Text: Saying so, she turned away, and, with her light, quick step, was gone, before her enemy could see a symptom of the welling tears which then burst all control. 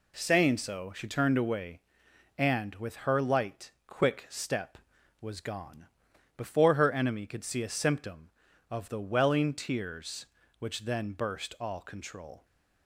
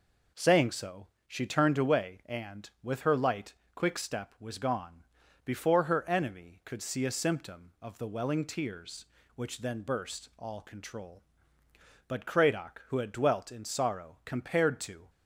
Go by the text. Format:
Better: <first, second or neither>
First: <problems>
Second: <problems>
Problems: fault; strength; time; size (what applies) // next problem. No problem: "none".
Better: first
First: none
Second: goes on to say "But Cradock who had dwelt in sorrow compared to"; strong; from 12.0 s on; 3.0 s long